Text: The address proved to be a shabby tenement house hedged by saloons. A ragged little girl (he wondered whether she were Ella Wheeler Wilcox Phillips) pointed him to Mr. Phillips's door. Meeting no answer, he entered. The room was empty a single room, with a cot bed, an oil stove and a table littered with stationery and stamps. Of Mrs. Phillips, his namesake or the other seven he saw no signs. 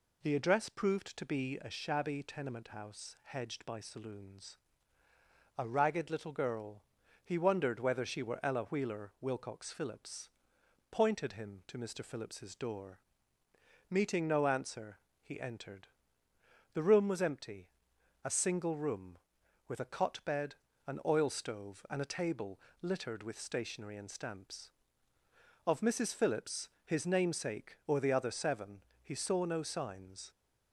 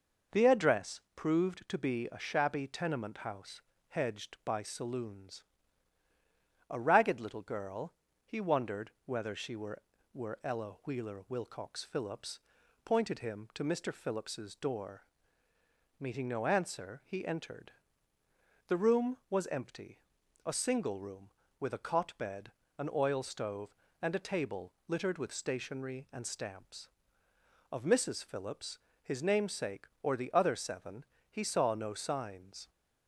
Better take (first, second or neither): first